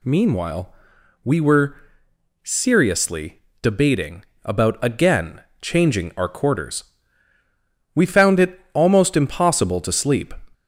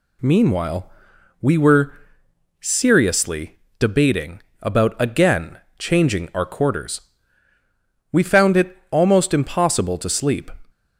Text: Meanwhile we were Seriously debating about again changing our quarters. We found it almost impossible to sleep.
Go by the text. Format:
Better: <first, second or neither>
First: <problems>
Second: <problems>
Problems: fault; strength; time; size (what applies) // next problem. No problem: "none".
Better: second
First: gets louder; slight; throughout; 3 dB // pauses between "Meanwhile" and "we"; noticeable; at 0.7 s; 0.50 s long // pauses between "were" and "Seriously"; noticeable; at 1.7 s; 0.68 s long // pauses between "Seriously" and "debating"; slight; at 3.3 s; 0.22 s long // pauses between "debating" and "about"; slight; at 4.2 s; 0.20 s long // pauses between "again" and "changing"; slight; at 5.4 s; 0.20 s long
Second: pauses between "Meanwhile" and "we"; noticeable; at 0.8 s; 0.50 s long // pauses between "were" and "Seriously"; noticeable; at 1.9 s; 0.68 s long // pauses between "Seriously" and "debating"; slight; at 3.5 s; 0.22 s long // pauses between "debating" and "about"; slight; at 4.4 s; 0.20 s long // pauses between "again" and "changing"; slight; at 5.5 s; 0.20 s long